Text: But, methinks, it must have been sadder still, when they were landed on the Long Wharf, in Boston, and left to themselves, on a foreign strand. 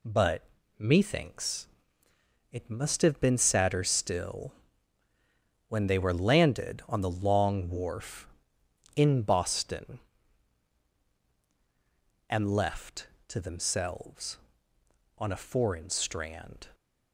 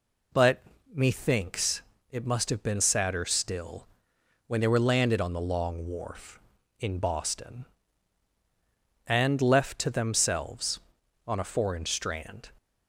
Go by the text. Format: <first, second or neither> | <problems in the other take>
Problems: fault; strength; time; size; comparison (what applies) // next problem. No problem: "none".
neither | none